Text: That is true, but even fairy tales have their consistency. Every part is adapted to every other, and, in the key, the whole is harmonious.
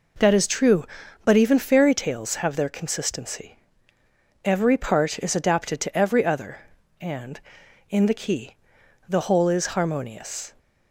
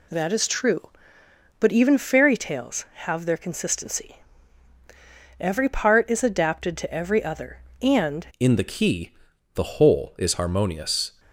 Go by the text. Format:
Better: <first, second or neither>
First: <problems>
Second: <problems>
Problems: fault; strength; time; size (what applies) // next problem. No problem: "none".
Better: first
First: none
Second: changes voice at "in"; from 8.3 s on; 2.8 s long